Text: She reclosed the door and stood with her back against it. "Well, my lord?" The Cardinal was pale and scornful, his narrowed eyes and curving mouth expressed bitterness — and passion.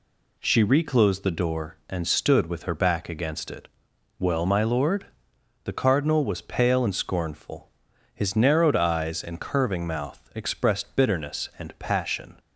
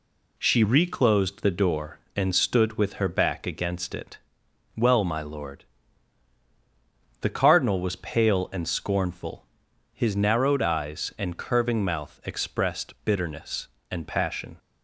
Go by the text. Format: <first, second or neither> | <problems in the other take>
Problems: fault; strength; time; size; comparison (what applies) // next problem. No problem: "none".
neither | none